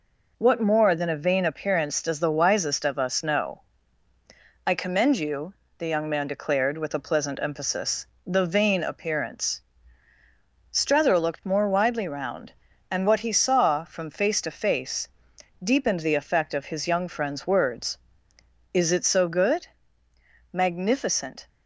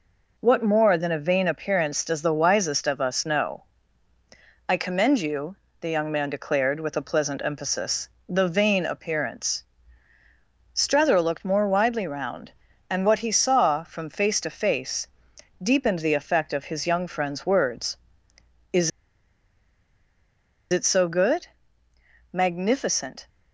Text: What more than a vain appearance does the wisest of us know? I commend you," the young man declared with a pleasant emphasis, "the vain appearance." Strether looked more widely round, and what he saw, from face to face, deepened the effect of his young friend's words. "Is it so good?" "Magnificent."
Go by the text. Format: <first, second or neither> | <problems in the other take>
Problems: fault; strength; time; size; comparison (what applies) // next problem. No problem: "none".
first | pauses between "Is" and "it"; strong; at 18.9 s; 1.8 s long